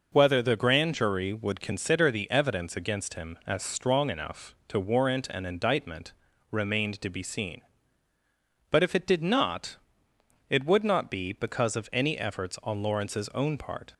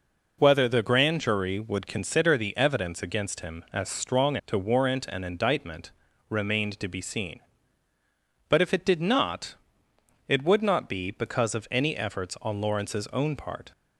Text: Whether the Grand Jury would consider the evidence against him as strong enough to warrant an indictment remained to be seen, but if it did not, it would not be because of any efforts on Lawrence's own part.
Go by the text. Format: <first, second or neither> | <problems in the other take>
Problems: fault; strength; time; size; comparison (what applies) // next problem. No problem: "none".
first | skips "enough"; at 4.4 s // pauses between "indictment" and "remained"; at 5.8 s; 0.40 s long; also in the first